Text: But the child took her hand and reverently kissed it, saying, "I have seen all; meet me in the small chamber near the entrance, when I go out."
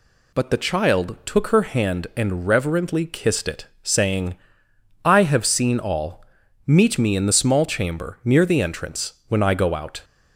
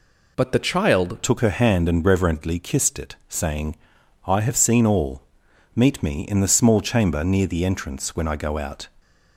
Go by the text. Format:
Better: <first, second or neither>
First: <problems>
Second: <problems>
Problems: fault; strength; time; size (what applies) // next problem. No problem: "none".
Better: first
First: none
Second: changes voice at "took"; from 1.2 s on; 7.6 s long